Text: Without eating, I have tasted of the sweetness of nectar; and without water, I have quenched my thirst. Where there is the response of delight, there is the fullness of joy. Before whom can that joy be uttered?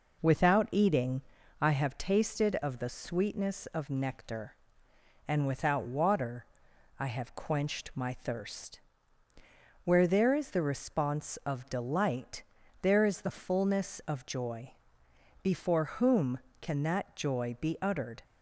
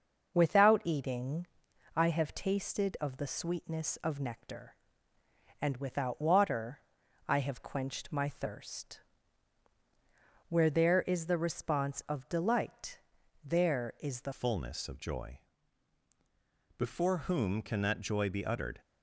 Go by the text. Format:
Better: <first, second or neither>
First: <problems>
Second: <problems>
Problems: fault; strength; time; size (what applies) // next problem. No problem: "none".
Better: first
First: none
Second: starts louder than the rest; noticeable; until 1.3 s; 6 dB // changes voice at "fullness"; from 14.3 s on; 4.5 s long